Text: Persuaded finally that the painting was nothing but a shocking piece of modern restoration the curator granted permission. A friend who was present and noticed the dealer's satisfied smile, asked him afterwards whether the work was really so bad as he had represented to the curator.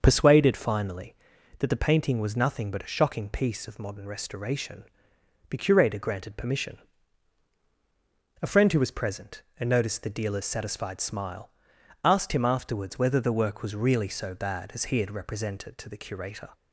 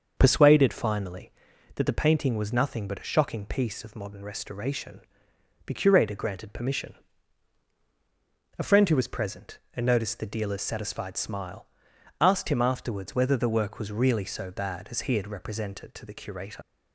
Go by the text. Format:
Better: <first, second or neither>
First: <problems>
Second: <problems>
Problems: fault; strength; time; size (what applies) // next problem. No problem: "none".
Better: first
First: starts louder than the rest; until 1.0 s; 6.5 dB // pauses between "restoration" and "the"; noticeable; at 4.8 s; 0.66 s long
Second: starts louder than the rest; until 1.1 s; 6.5 dB // pauses between "restoration" and "the"; noticeable; at 5.0 s; 0.66 s long // leaves "curator" unfinished; at 16.6 s; 85 ms